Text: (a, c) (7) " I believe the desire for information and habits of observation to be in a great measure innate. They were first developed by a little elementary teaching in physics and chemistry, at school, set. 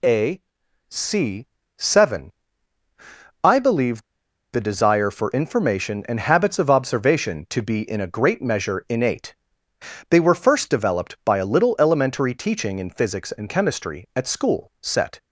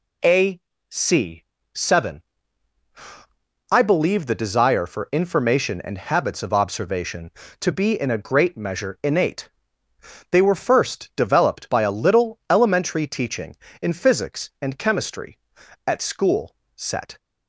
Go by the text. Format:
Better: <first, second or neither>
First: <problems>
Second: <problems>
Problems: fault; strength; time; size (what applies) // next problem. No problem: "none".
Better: second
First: pauses between "believe" and "the"; noticeable; at 4.0 s; 0.49 s long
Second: none